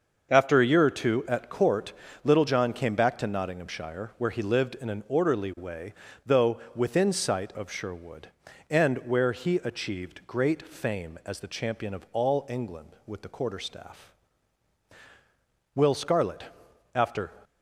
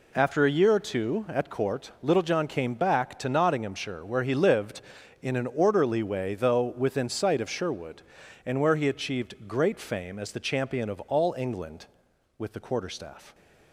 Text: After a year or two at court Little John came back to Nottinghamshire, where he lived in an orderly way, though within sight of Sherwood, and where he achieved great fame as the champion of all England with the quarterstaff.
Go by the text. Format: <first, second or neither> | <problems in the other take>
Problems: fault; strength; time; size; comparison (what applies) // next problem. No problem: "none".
second | starts louder than the rest; until 1.3 s; 6.5 dB // pauses between "court" and "Little"; slight; at 1.9 s; 0.32 s long // pauses between "though" and "within"; slight; at 6.5 s; 0.16 s long // goes on to say "Will Scarlet after"; from 15.7 s on; 1.5 s long